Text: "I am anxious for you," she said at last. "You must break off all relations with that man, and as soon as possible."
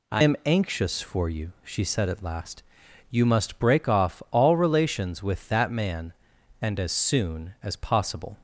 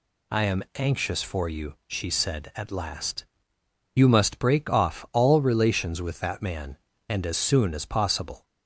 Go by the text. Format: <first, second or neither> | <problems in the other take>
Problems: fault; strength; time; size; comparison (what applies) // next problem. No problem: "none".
second | changes voice at "am"; from 0.2 s on; 8.1 s long